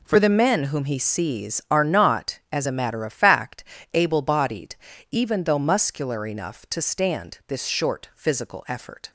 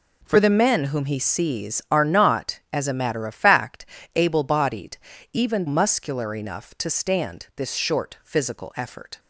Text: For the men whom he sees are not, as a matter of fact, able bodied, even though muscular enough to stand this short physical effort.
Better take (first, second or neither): first